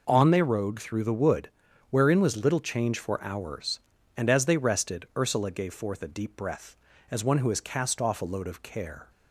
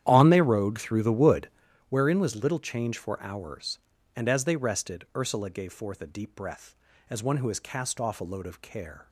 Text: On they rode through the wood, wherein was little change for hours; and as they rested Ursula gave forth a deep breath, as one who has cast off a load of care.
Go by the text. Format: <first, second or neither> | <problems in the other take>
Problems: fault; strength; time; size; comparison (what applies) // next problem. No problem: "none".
first | starts louder than the rest; strong; until 1.7 s; 10.5 dB